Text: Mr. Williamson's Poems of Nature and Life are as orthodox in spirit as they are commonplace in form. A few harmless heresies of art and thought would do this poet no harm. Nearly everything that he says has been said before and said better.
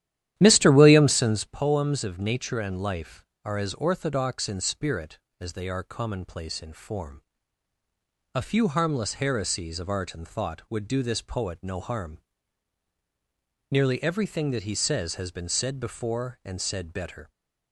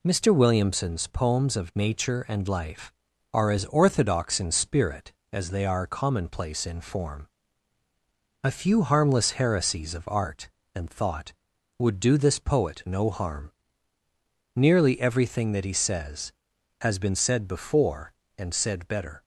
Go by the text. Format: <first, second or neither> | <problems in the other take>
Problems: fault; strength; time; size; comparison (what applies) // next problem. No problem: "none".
second | starts louder than the rest; strong; until 1.6 s; 12 dB